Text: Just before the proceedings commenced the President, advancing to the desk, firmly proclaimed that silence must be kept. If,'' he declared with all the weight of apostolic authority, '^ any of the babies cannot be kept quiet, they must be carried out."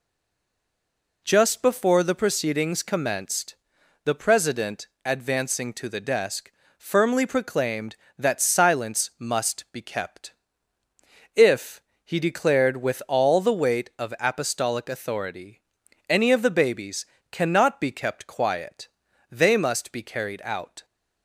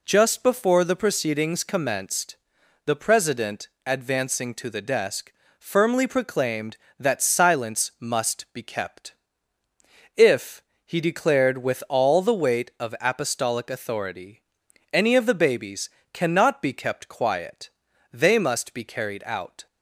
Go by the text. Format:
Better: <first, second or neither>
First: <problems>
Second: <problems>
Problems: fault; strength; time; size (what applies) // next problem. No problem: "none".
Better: second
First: stays silent before the first word; noticeable; until 1.2 s; 1.2 s long // pauses between "commenced" and "the"; noticeable; at 3.5 s; 0.50 s long // pauses between "babies" and "cannot"; slight; at 17.0 s; 0.26 s long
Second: pauses between "commenced" and "the"; noticeable; at 2.3 s; 0.50 s long // pauses between "babies" and "cannot"; slight; at 15.8 s; 0.24 s long